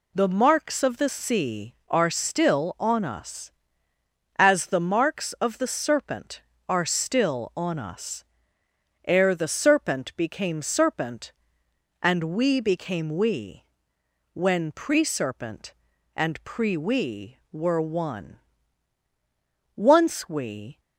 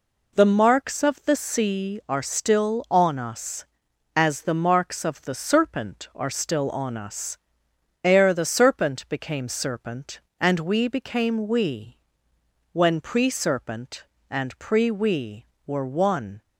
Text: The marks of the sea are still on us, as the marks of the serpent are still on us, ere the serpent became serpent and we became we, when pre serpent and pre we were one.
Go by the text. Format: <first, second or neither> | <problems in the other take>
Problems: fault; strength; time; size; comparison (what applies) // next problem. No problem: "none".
second | goes on to say "Once we"; noticeable; from 19.7 s on; 1.0 s long